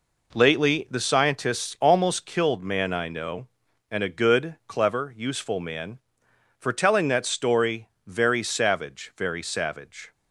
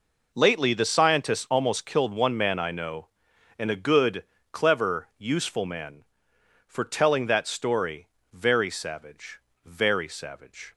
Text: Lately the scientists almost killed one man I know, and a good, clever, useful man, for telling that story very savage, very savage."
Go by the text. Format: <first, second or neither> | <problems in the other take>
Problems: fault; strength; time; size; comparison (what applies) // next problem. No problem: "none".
second | skips "one"; at 2.6 s // pauses between "story" and "very"; slight; at 7.8 s; 0.18 s long; slight in the second